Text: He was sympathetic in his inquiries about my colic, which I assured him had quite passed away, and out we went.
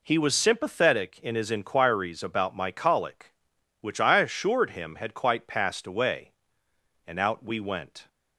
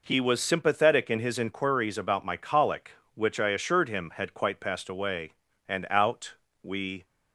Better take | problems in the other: first | pauses between "out" and "we"; slight; at 6.3 s; 0.28 s long // stops before "went"; at 7.0 s

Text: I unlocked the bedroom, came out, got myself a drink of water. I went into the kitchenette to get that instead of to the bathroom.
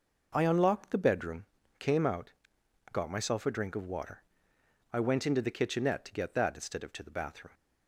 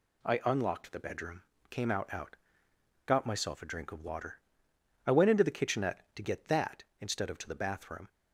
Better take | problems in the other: first | says "out" twice; at 2.1 s

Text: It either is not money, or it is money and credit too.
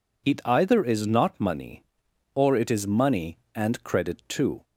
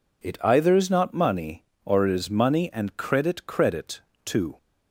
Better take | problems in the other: first | says "credit" twice; at 3.4 s

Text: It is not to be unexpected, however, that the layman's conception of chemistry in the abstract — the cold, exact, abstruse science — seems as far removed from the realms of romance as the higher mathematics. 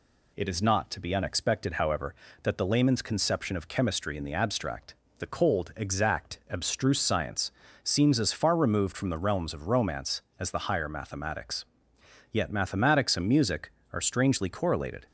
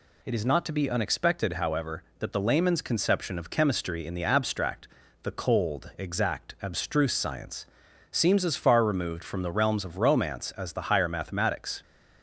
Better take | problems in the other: second | goes on to say "Yet mathematics and music are strangely correlated"; strong; from 12.2 s on; 2.7 s long

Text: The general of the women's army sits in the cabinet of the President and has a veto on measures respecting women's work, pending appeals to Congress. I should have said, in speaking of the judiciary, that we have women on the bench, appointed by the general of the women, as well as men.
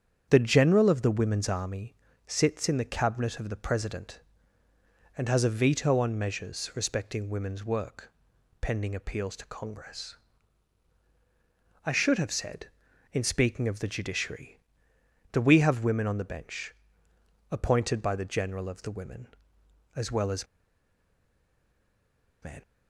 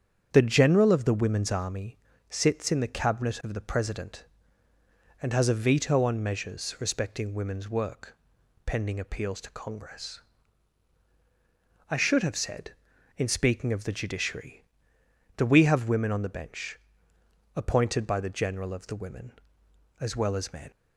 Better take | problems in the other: second | starts louder than the rest; strong; until 1.3 s; 8 dB; strong in the second // pauses between "army" and "sits"; slight; at 1.9 s; 0.32 s long; slight in the second // pauses between "as" and "men"; strong; at 20.4 s; 1.9 s long

